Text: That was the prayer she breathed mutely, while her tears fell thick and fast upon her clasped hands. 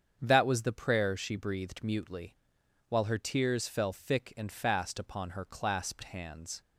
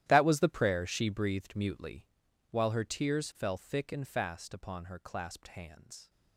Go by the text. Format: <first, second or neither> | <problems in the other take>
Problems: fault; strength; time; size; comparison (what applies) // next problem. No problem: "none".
first | gets quieter; strong; throughout; 17.5 dB // starts louder than the rest; strong; until 1.0 s; 13 dB; strong in the first